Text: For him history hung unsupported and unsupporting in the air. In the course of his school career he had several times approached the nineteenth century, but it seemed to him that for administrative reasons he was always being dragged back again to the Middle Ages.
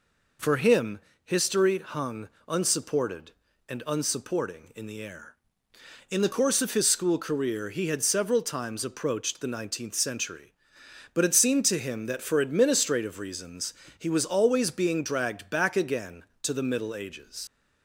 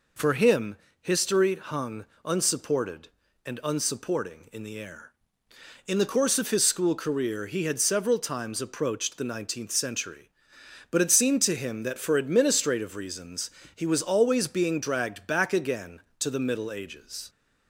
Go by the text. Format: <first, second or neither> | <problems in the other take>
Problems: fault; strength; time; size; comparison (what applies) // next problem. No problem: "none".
second | pauses between "him" and "history"; slight; at 1.0 s; 0.22 s long; slight in the second // pauses between "hung" and "unsupported"; slight; at 2.2 s; 0.20 s long; slight in the second // pauses between "reasons" and "he"; slight; at 13.7 s; 0.24 s long; slight in the second // leaves "Ages" unfinished; at 17.4 s; 50 ms